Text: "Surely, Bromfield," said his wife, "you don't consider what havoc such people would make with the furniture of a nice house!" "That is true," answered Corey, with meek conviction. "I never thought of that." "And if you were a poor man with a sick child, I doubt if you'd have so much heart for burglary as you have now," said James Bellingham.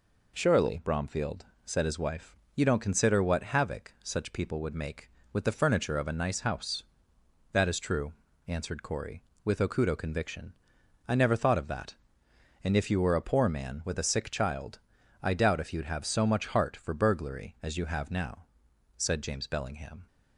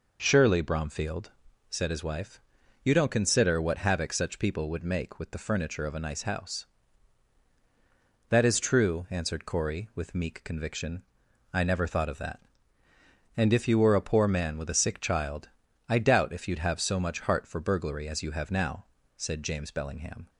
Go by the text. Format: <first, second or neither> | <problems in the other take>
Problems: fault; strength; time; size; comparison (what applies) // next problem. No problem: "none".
second | says "okudo" for "meek"; at 9.6 s